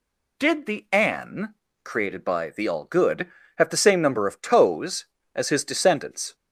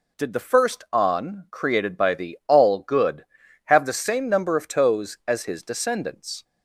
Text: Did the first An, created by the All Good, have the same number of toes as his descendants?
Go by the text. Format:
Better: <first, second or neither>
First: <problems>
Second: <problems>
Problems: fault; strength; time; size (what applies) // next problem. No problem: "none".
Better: second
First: skips "first"; at 0.8 s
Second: none